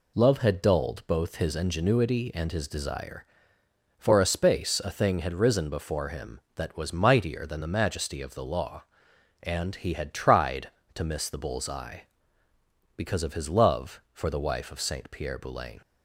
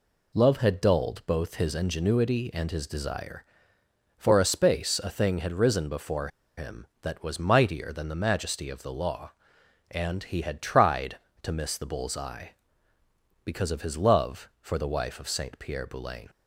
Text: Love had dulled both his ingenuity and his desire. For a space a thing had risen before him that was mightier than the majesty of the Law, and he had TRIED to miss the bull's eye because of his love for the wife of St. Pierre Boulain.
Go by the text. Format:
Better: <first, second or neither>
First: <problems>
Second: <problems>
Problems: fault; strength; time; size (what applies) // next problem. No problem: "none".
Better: first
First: none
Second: pauses between "before" and "him"; slight; at 6.2 s; 0.28 s long